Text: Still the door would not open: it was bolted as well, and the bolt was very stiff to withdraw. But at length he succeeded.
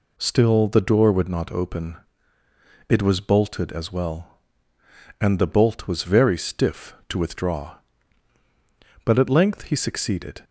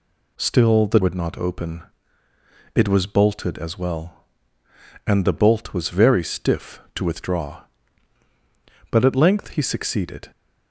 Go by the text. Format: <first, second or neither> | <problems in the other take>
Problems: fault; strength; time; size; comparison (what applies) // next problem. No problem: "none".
first | skips "door"; at 1.0 s